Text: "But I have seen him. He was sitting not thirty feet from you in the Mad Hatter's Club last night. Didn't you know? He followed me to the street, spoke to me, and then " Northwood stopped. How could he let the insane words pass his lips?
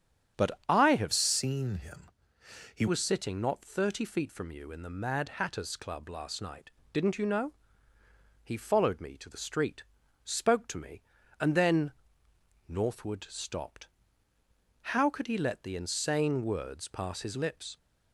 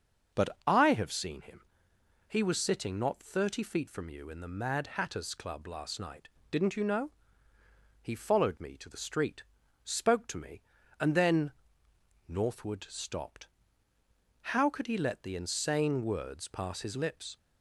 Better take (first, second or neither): second